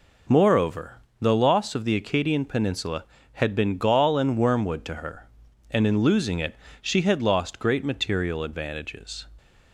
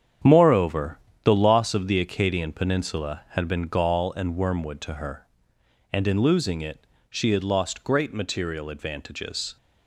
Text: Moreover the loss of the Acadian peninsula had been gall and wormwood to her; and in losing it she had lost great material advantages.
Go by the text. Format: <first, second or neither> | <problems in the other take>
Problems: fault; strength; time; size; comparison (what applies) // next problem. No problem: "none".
first | gets quieter; strong; throughout; 9.5 dB // pauses between "Moreover" and "the"; slight; at 0.9 s; 0.26 s long; slight in the first // pauses between "it" and "she"; slight; at 6.8 s; 0.24 s long; slight in the first